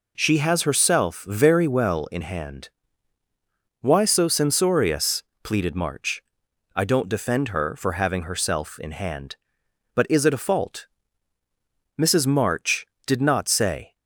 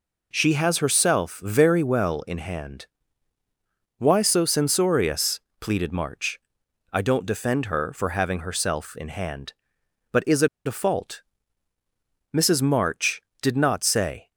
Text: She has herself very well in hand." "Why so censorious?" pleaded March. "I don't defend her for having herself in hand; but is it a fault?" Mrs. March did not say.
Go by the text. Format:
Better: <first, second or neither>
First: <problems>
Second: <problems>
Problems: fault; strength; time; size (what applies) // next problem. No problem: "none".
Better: first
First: none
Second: pauses between "it" and "a"; slight; at 10.4 s; 0.18 s long